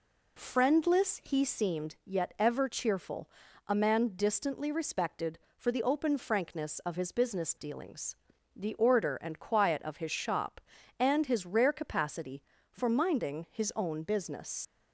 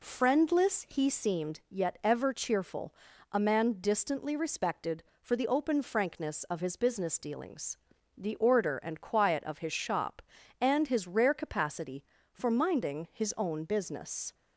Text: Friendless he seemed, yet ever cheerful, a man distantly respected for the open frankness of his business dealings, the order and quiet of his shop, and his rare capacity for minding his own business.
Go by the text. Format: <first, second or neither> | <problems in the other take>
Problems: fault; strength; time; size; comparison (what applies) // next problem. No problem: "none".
second | leaves "business" unfinished; at 14.6 s; 75 ms